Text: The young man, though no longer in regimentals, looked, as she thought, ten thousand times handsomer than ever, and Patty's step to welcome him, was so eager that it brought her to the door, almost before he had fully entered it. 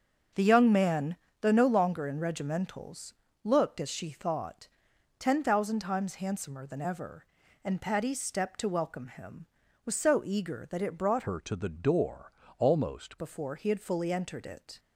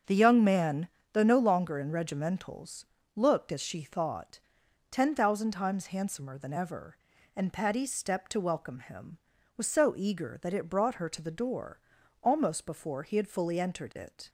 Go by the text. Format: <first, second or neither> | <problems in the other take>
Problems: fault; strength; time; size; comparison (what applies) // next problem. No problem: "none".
second | starts louder than the rest; until 1.5 s; 6.5 dB; also in the second // changes voice from "her" to "almost"; from 11.2 to 13.1 s; 1.9 s long